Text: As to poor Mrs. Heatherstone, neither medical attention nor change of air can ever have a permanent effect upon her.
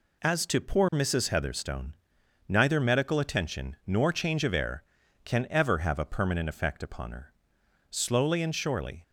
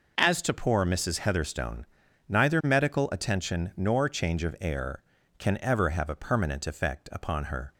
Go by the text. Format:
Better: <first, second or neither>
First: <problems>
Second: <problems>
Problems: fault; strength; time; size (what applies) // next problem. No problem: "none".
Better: second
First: goes on to say "Slowly and surely"; noticeable; from 7.9 s on; 1.1 s long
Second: none